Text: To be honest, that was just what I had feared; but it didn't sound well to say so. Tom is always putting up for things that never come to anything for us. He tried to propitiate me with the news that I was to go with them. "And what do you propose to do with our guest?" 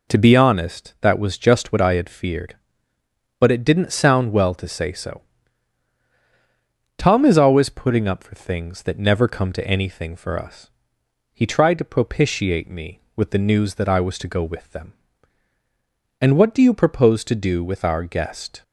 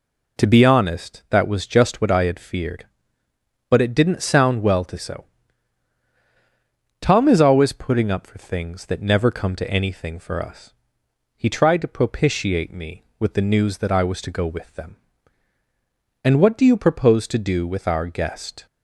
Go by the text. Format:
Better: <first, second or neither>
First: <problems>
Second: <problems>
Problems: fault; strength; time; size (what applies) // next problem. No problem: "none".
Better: first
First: none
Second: skips "say"; at 4.9 s